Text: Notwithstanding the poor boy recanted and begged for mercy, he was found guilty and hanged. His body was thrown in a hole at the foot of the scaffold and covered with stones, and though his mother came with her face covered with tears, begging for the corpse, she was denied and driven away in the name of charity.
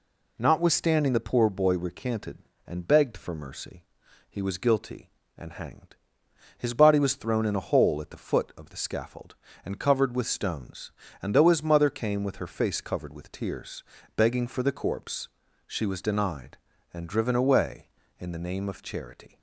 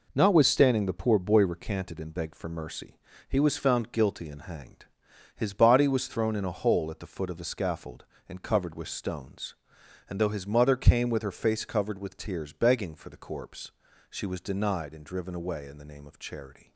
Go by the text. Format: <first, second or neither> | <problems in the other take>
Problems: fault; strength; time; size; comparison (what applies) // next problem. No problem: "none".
second | skips "found"; at 4.5 s